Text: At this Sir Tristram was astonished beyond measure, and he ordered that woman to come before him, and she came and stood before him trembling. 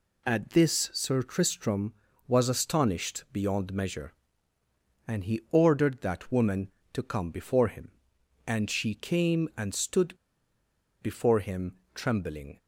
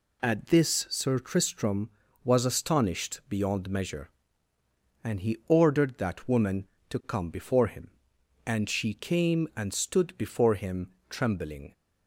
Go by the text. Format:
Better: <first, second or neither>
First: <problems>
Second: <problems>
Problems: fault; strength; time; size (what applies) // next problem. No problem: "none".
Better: second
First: pauses between "stood" and "before"; noticeable; at 10.1 s; 0.88 s long // pauses between "him" and "trembling"; slight; at 11.7 s; 0.16 s long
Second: pauses between "him" and "trembling"; slight; at 10.9 s; 0.16 s long